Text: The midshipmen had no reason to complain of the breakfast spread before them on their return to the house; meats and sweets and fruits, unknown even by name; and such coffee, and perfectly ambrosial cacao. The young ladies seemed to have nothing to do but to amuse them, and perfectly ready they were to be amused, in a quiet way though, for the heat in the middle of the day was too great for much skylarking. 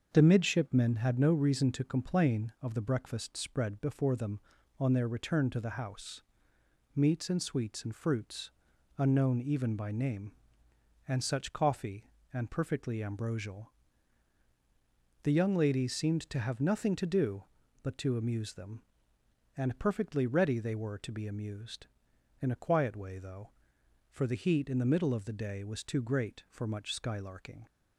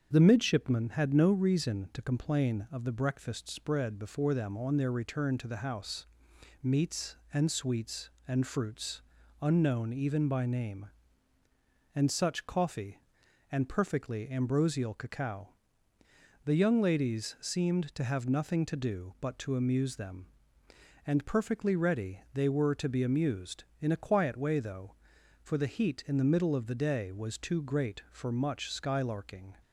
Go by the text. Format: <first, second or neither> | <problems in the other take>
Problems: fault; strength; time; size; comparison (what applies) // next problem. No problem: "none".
second | starts louder than the rest; until 1.1 s; 6.5 dB; strong in the second // skips "cacao"; at 14.4 s